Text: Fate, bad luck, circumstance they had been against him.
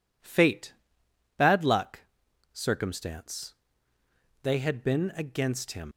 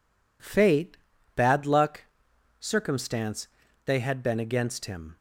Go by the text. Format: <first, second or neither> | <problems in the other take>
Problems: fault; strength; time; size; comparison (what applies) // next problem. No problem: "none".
second | pauses between "circumstance" and "they"; noticeable; at 3.5 s; 0.88 s long; also in the second // leaves "him" unfinished; at 5.9 s; 90 ms